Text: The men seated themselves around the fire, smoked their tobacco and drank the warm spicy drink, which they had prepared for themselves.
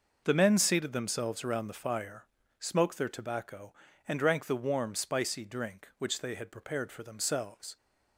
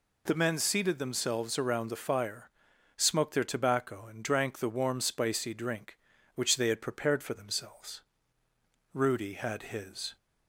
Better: first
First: none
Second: goes on to say "Rudy had his"; noticeable; from 8.9 s on; 1.2 s long

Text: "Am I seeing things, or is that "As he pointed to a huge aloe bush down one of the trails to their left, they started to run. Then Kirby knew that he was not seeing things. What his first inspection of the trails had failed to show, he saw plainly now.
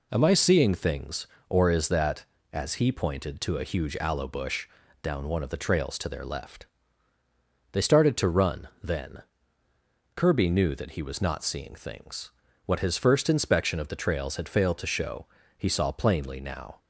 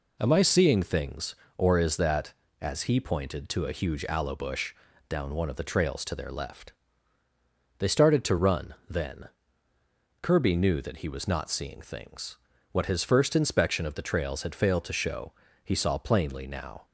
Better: neither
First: pauses between "bush" and "down"; slight; at 4.6 s; 0.36 s long // pauses between "Then" and "Kirby"; noticeable; at 9.2 s; 0.92 s long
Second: pauses between "bush" and "down"; slight; at 4.7 s; 0.36 s long // pauses between "Then" and "Kirby"; noticeable; at 9.2 s; 0.92 s long

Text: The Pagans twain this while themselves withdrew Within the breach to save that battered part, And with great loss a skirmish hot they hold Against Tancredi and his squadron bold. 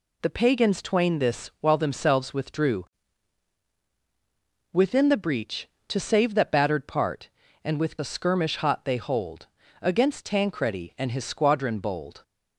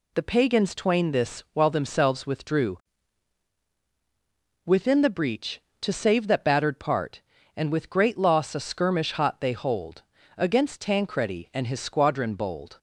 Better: second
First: pauses between "withdrew" and "Within"; strong; at 2.8 s; 1.9 s long // skips "great loss"; at 7.9 s // pauses between "hold" and "Against"; slight; at 9.4 s; 0.34 s long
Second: pauses between "withdrew" and "Within"; strong; at 2.7 s; 1.9 s long // pauses between "hold" and "Against"; slight; at 10.0 s; 0.34 s long

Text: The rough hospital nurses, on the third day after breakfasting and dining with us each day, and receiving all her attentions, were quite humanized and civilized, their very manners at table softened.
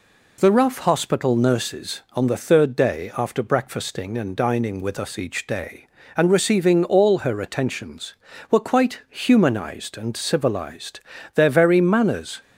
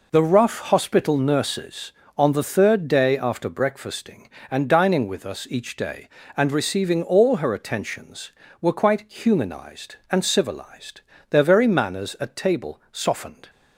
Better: second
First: stops before "at table softened"; at 12.4 s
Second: none

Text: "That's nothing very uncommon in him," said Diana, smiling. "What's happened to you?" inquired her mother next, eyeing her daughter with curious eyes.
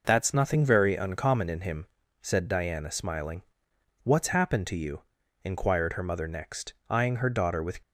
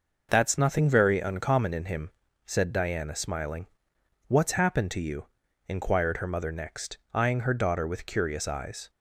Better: second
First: stops before "curious eyes"; at 7.8 s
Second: none

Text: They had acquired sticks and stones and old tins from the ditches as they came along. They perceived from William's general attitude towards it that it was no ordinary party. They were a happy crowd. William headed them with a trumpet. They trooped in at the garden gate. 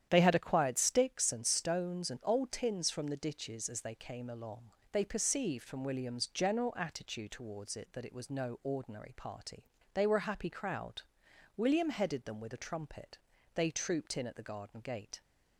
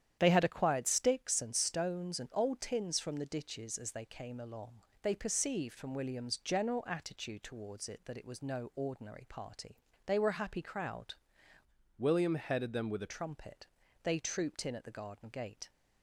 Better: first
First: starts louder than the rest; strong; until 1.1 s; 10 dB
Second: starts louder than the rest; strong; until 1.2 s; 10 dB // changes voice from "William" to "a"; from 11.9 to 13.1 s; 1.2 s long

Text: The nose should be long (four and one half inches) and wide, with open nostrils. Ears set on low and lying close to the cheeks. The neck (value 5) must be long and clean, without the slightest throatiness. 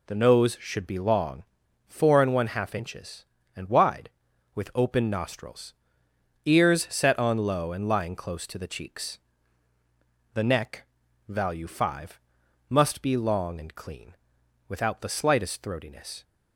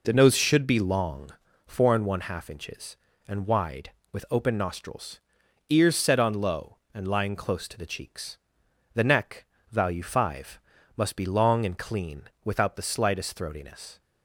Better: neither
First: none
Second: none

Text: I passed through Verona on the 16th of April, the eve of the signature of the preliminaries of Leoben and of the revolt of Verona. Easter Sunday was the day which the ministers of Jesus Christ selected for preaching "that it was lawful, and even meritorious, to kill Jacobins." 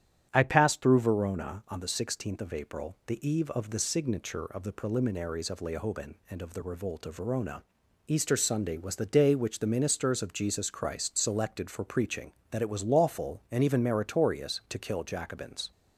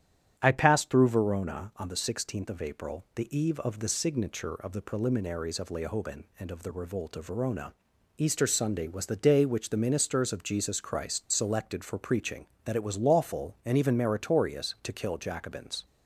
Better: neither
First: starts louder than the rest; strong; until 1.3 s; 9.5 dB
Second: starts louder than the rest; strong; until 1.4 s; 10 dB

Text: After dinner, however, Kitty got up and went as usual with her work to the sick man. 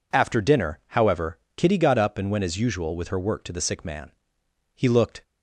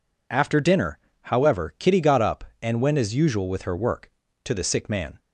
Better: second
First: goes on to say "He looked"; slight; from 4.7 s on; 0.48 s long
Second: none

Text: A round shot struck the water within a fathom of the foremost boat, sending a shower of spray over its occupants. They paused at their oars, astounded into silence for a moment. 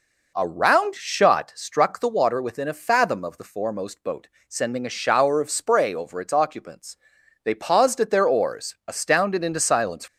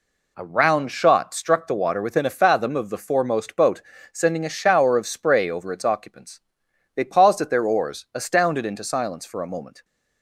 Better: second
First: stops before "for a moment"; at 10.0 s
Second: none

